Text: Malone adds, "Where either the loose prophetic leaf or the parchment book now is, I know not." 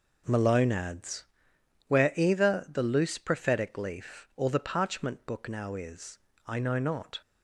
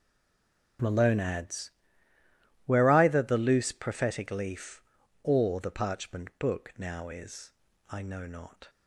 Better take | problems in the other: first | stays silent before the first word; slight; until 0.7 s; 0.7 s long

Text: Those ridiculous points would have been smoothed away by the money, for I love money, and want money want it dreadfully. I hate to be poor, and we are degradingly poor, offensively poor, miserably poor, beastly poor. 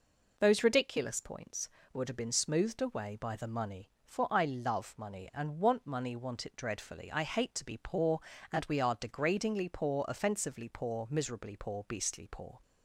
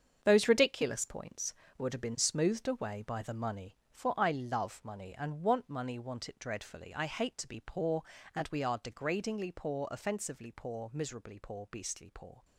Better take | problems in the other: first | gets quieter; strong; throughout; 9 dB

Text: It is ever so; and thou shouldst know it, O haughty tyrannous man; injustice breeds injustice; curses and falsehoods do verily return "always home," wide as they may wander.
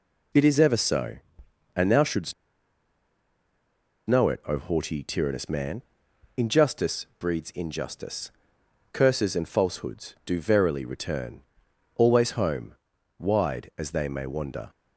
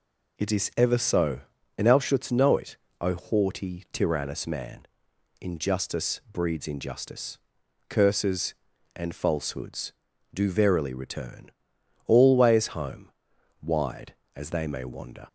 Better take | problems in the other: second | pauses between "shouldst" and "know"; strong; at 2.3 s; 1.7 s long // pauses between "return" and "always"; noticeable; at 11.4 s; 0.54 s long; noticeable in the second

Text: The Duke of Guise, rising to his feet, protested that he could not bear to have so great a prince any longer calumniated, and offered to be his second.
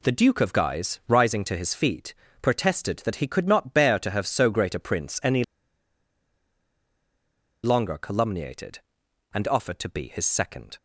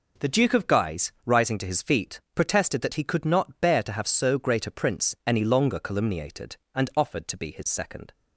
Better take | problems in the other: second | pauses between "any" and "longer"; strong; at 5.4 s; 2.1 s long

